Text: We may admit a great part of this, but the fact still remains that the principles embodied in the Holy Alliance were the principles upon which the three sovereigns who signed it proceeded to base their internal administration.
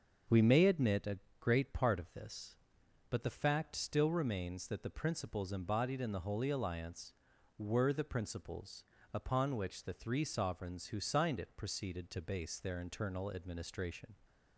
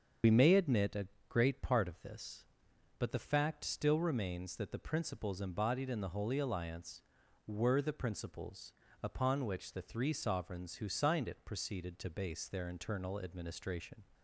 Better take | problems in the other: first | loses the start of "We"; at 0.2 s; 60 ms // starts louder than the rest; strong; until 1.4 s; 7 dB; also in the first // pauses between "a" and "great"; slight; at 1.0 s; 0.22 s long; slight in the first // pauses between "principles" and "upon"; slight; at 8.7 s; 0.30 s long; slight in the first

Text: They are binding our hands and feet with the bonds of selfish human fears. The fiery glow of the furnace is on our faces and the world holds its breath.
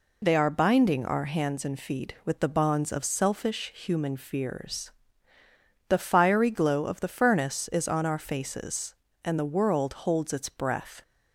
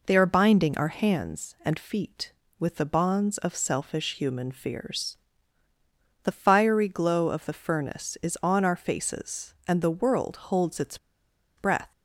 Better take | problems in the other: first | pauses between "its" and "breath"; noticeable; at 10.9 s; 0.60 s long

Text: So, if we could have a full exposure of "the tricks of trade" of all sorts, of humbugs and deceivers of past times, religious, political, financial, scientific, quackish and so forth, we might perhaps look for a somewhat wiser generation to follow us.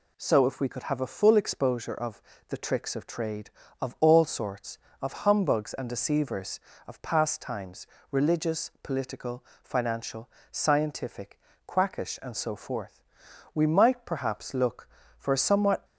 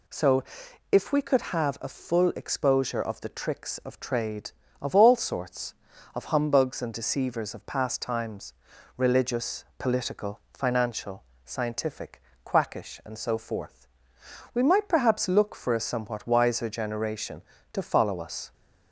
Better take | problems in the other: second | pauses between "of" and "the"; slight; at 2.2 s; 0.26 s long // stops before "wiser generation to follow us"; at 15.8 s

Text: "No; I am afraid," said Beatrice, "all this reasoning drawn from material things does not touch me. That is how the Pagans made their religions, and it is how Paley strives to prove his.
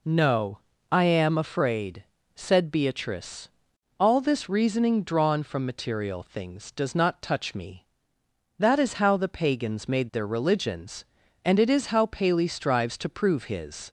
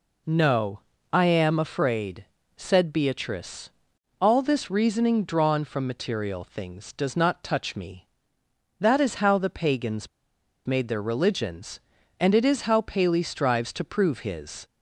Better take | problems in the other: first | pauses between "Pagans" and "made"; noticeable; at 10.0 s; 0.59 s long

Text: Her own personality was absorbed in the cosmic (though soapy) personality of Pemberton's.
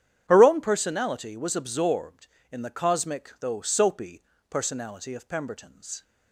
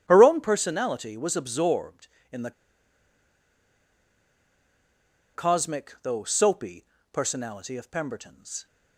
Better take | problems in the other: first | starts louder than the rest; strong; until 1.0 s; 9.5 dB; strong in the first // pauses between "the" and "cosmic"; strong; at 2.5 s; 2.8 s long

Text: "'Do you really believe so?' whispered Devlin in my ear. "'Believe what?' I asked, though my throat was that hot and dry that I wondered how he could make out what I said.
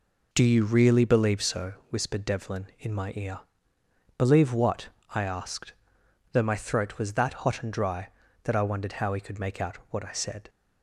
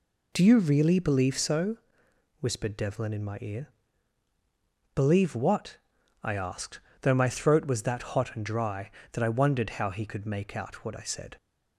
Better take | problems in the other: neither | none

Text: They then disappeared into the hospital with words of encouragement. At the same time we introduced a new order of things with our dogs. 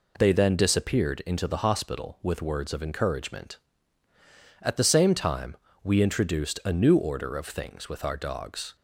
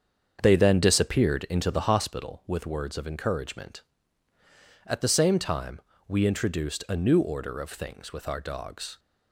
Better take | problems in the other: first | starts louder than the rest; strong; until 2.2 s; 7 dB // pauses between "time" and "we"; slight; at 5.7 s; 0.28 s long; slight in the first

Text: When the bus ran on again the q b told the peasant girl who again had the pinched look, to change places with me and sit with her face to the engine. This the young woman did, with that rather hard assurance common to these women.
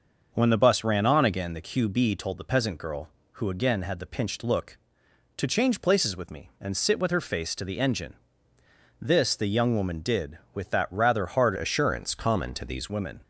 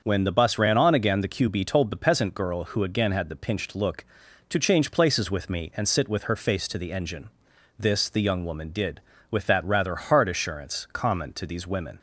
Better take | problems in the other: second | starts louder than the rest; until 1.3 s; 6 dB; also in the second // changes voice from "assurance" to "these"; from 11.5 to 12.8 s; 1.3 s long

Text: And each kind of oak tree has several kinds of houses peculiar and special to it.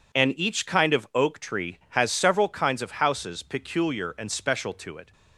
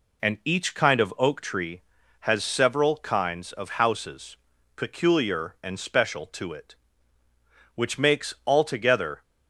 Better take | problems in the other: first | pauses between "houses" and "peculiar"; at 4.3 s; 0.40 s long // goes on to say "Which makes altogether"; from 7.7 s on; 1.4 s long

